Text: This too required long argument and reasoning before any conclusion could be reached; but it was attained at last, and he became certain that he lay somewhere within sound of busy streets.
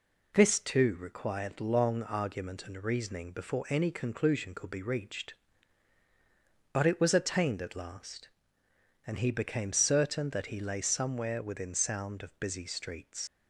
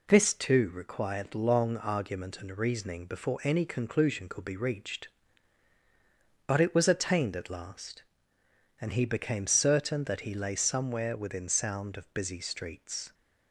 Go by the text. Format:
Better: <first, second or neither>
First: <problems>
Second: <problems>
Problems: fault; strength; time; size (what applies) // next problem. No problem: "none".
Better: second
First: leaves "streets" unfinished; at 13.2 s; 125 ms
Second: none